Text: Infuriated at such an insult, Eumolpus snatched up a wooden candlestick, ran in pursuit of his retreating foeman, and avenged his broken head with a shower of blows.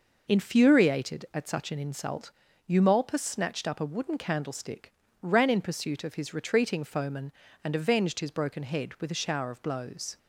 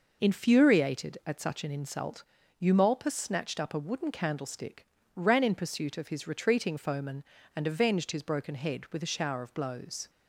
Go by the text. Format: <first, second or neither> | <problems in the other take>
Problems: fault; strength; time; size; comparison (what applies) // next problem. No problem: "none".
neither | none